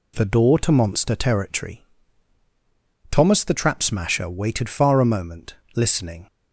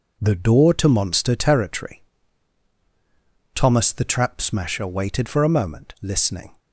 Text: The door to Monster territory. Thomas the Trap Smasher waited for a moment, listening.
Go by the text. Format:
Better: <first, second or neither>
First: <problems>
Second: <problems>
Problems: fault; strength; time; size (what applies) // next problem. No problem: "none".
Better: second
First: says "far" for "for"; at 4.6 s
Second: none